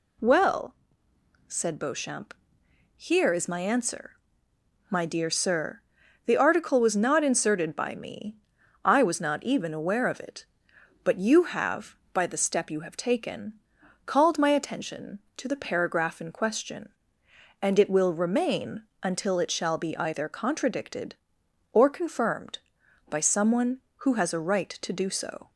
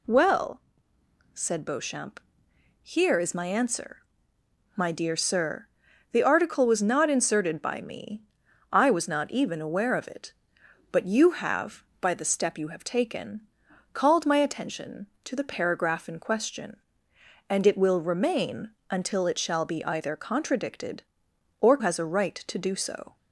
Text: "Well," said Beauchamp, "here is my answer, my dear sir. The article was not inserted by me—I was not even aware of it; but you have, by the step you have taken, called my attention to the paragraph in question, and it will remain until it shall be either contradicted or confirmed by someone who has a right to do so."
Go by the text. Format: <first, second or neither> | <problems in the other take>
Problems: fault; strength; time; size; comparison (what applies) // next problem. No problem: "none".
first | pauses between "remain" and "until"; slight; at 18.7 s; 0.18 s long; slight in the first // skips "confirmed by someone who"; at 21.7 s